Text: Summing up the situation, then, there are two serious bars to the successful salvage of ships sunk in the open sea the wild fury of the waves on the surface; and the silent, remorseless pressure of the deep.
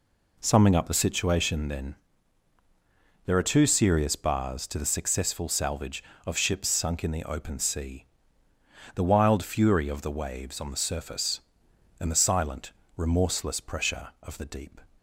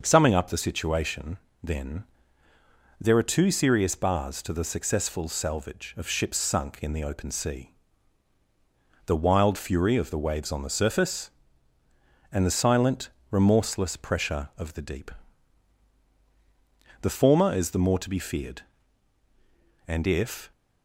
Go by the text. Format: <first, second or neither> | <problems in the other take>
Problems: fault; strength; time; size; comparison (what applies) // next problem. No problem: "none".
first | starts louder than the rest; noticeable; until 1.0 s; 6 dB // pauses between "sea" and "the"; strong; at 7.6 s; 1.4 s long; noticeable in the first // goes on to say "The former is the more to be feared and if"; strong; from 17.0 s on; 3.5 s long